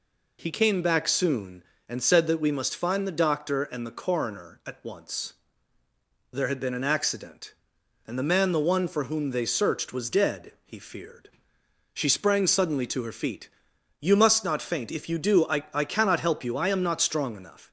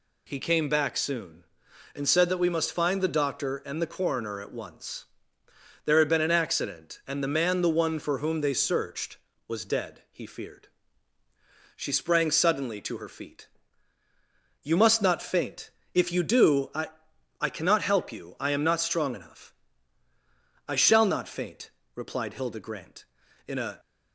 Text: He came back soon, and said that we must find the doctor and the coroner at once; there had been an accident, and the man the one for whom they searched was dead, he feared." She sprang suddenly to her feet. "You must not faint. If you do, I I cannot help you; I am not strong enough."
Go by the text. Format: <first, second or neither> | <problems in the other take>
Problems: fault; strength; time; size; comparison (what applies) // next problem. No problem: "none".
first | pauses between "I" and "I"; noticeable; at 16.8 s; 0.50 s long // goes on to say "I shall not faint replied Hilda Grant in a"; strong; from 20.6 s on; 3.1 s long